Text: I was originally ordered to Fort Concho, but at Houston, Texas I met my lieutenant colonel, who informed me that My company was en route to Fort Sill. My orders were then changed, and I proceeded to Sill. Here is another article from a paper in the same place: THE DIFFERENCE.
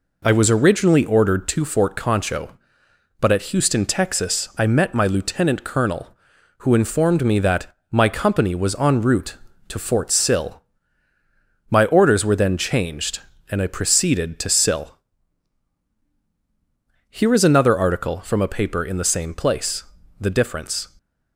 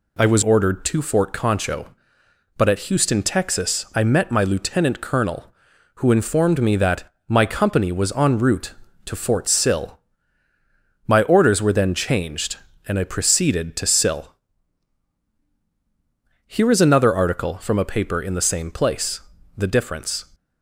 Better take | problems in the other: first | skips "originally"; at 0.4 s // pauses between "that" and "My"; slight; at 7.0 s; 0.22 s long; slight in the first

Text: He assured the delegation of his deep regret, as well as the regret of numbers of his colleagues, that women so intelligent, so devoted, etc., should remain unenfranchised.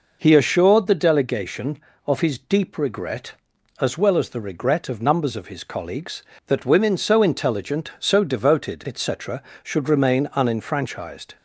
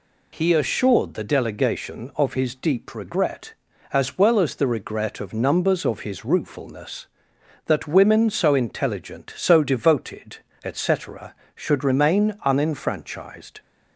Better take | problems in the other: first | says "ruefulness" for "colleagues"; at 6.2 s

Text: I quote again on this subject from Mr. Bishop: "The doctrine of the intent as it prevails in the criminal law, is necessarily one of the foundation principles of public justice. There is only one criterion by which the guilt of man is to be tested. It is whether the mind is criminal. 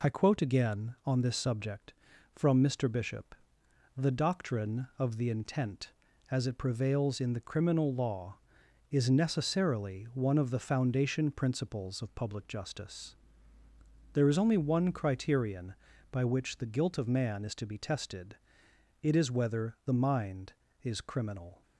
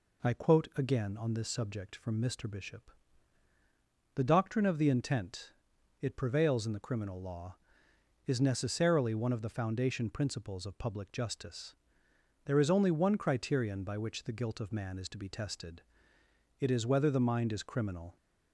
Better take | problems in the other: first | skips "as"; at 5.7 s

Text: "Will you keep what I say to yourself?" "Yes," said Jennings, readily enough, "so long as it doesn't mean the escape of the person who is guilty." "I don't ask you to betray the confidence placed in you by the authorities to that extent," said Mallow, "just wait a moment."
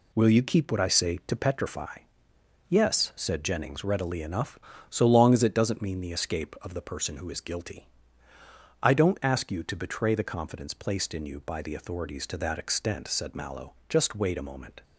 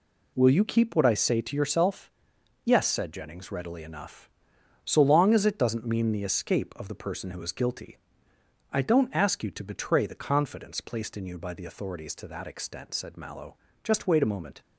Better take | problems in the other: second | says "petrify" for "yourself"; at 1.3 s

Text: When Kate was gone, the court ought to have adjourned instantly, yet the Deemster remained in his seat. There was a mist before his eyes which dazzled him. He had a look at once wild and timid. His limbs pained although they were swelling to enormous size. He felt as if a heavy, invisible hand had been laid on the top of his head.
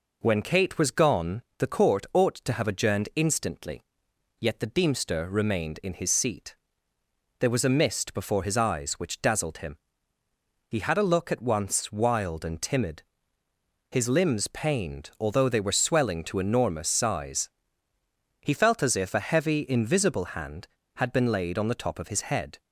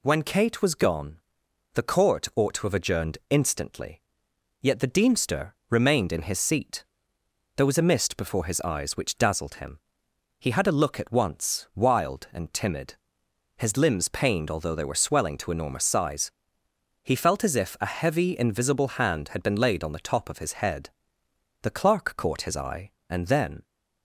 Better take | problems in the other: first | pauses between "Deemster" and "remained"; slight; at 5.5 s; 0.16 s long // goes on to say "The clerk caught his eye and then"; strong; from 21.6 s on; 2.0 s long

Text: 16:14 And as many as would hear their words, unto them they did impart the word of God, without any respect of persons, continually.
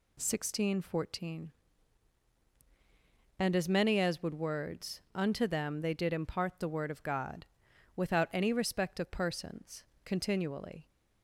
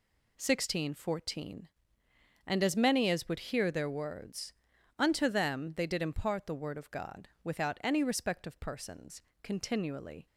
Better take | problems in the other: second | skips "hear their"; at 4.3 s

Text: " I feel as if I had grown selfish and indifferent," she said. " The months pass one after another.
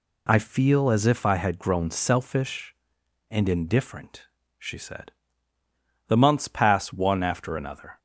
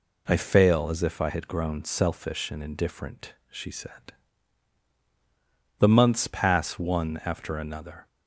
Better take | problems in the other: first | says "fail" for "feel"; at 0.3 s

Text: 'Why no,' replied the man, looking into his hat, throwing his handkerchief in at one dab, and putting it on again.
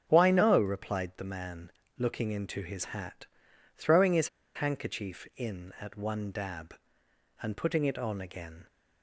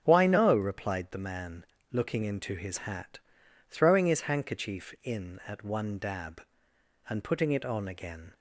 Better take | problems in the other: second | starts louder than the rest; until 1.0 s; 7 dB; also in the second // pauses between "his" and "handkerchief"; slight; at 4.2 s; 0.26 s long

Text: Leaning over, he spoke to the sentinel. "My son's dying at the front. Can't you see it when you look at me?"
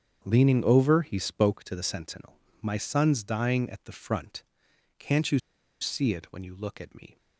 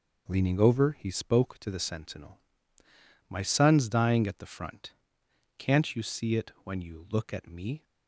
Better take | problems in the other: second | starts louder than the rest; strong; until 1.2 s; 7.5 dB // pauses between "you" and "see"; at 5.3 s; 0.41 s long

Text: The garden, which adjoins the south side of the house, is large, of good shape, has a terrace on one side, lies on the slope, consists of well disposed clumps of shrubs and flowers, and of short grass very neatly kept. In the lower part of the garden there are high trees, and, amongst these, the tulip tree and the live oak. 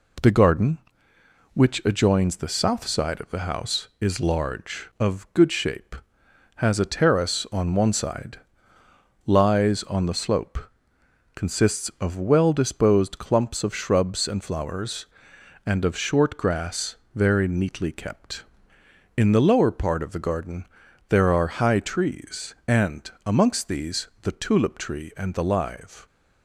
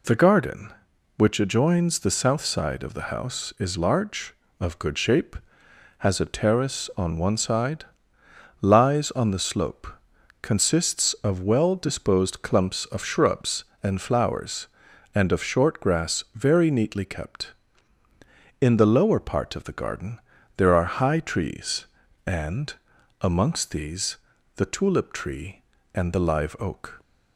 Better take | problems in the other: second | pauses between "grass" and "very"; slight; at 16.9 s; 0.20 s long // pauses between "garden" and "there"; at 20.6 s; 0.44 s long; also in the second // stops before "oak"; at 26.0 s

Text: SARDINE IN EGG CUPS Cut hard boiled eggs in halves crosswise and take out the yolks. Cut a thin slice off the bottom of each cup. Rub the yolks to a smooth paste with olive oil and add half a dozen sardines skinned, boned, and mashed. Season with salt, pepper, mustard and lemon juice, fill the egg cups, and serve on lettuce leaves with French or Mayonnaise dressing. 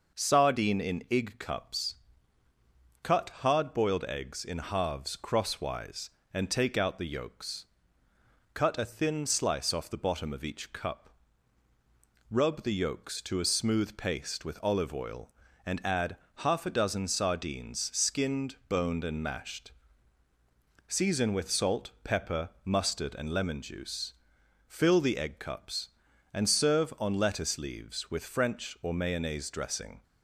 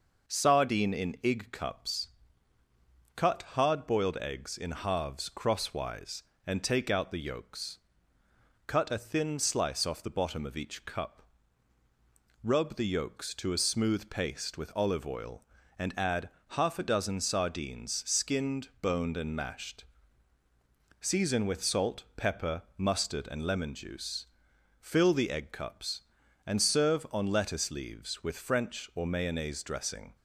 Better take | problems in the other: neither | pauses between "CUPS" and "Cut"; the same in both // pauses between "add" and "half"; slight; the same in both

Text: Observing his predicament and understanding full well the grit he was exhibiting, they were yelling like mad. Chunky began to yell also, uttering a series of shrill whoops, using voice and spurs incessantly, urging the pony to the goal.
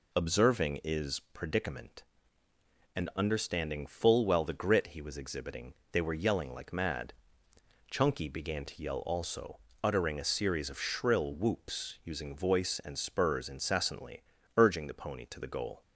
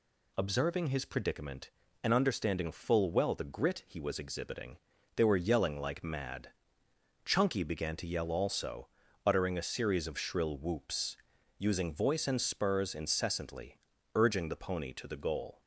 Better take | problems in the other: second | says "is" for "his"; at 0.8 s

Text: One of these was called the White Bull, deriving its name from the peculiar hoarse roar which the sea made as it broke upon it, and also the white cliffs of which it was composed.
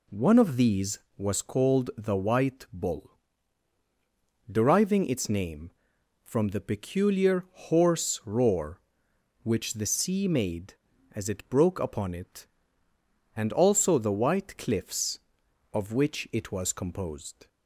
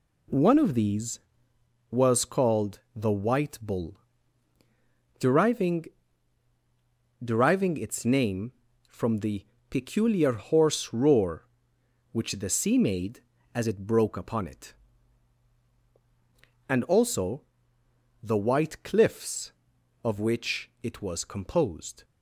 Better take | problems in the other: first | says "deriving" twice; at 7.2 s // pauses between "the" and "peculiar"; slight; at 9.4 s; 0.28 s long // pauses between "also" and "the"; noticeable; at 17.4 s; 0.80 s long

